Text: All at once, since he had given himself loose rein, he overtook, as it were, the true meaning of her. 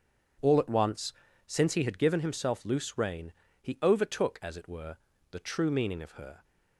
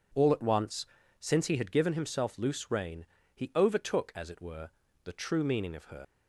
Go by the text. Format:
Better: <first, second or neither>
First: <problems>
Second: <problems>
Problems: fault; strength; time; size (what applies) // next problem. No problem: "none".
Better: first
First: none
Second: leaves "her" unfinished; at 6.0 s; 115 ms